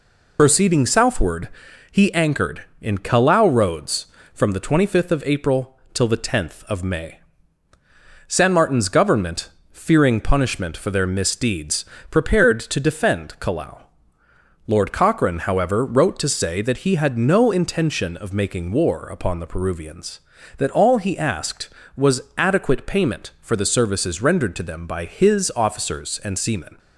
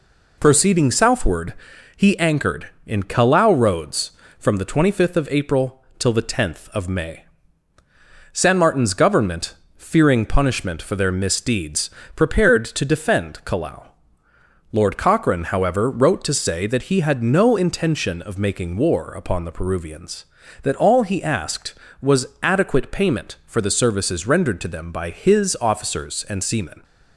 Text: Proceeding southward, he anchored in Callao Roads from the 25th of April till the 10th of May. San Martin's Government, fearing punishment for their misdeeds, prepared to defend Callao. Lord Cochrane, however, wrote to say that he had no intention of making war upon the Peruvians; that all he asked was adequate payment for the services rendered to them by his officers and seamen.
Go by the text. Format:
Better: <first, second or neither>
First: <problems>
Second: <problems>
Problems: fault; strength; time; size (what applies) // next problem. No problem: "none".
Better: second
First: loses the start of "Proceeding"; at 0.3 s; 60 ms // pauses between "April" and "till"; slight; at 5.7 s; 0.16 s long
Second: pauses between "April" and "till"; slight; at 5.8 s; 0.16 s long